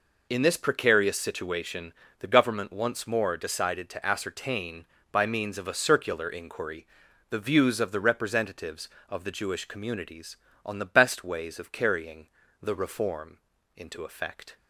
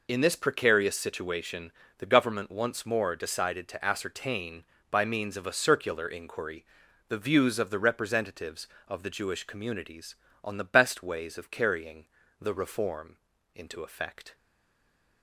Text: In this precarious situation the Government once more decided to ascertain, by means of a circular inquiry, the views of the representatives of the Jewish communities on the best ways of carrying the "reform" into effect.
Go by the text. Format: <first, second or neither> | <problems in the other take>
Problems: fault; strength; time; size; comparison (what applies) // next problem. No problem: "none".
first | pauses between "situation" and "the"; slight; at 1.7 s; 0.28 s long; slight in the first // pauses between "carrying" and "the"; slight; at 12.0 s; 0.34 s long; slight in the first // pauses between "reform" and "into"; at 13.1 s; 0.40 s long; also in the first // stays silent after the last word; slight; from 14.3 s on; 0.9 s long